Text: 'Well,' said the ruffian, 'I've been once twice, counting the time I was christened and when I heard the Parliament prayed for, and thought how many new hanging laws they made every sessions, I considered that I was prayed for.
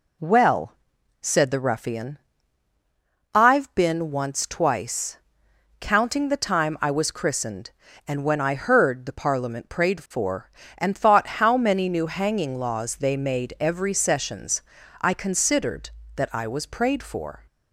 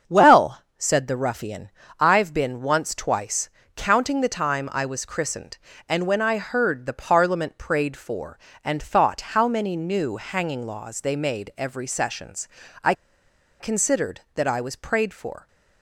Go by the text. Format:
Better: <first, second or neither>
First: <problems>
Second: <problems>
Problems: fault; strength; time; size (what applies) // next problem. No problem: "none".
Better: first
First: none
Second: starts louder than the rest; strong; until 1.2 s; 7 dB // pauses between "I" and "considered"; noticeable; at 12.9 s; 0.67 s long